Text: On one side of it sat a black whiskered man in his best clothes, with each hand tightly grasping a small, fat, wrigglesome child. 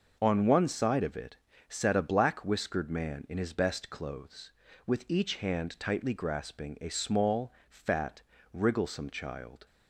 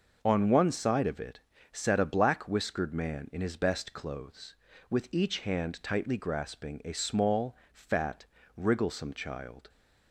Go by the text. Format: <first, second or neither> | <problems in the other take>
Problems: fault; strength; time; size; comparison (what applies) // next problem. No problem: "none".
neither | pauses between "it" and "sat"; slight; the same in both